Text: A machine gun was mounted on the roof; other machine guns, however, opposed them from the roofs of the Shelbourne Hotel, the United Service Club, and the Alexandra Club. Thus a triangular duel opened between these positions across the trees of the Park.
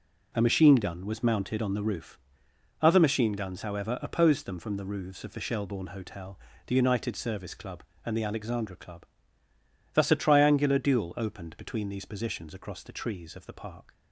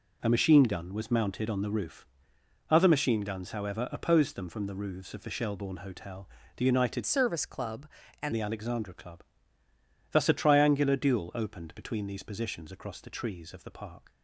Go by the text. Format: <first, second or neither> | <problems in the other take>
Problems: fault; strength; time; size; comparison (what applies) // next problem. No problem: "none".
first | changes voice from "Service" to "and"; from 7.0 to 8.3 s; 1.3 s long